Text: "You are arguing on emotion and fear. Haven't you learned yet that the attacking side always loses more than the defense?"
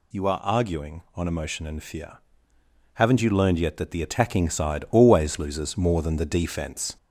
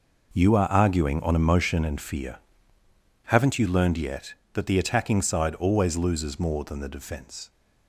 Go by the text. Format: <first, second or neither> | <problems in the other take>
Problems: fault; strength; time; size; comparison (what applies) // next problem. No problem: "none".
second | gets louder; slight; throughout; 2.5 dB